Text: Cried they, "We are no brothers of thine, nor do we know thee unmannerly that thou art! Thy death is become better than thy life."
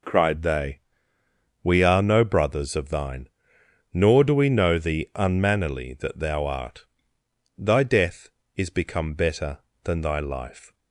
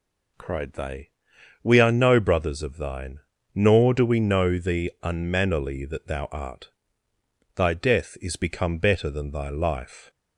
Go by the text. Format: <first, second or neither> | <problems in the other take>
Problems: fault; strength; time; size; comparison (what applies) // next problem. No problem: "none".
neither | none